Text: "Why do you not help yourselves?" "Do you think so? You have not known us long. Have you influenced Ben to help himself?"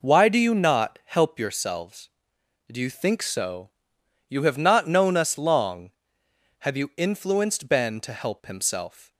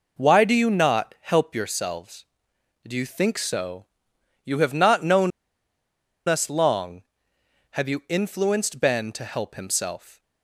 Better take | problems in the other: first | pauses between "known" and "us"; noticeable; at 5.3 s; 0.96 s long

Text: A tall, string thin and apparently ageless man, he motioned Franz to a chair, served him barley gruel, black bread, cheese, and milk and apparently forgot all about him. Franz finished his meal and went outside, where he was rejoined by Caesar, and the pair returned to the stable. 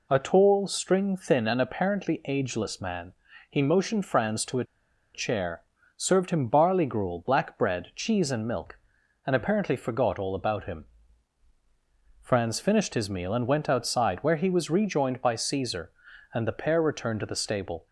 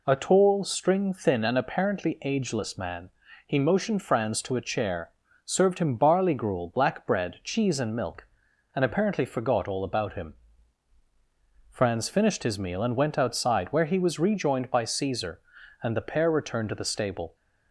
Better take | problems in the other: second | pauses between "a" and "chair"; noticeable; at 4.6 s; 0.50 s long

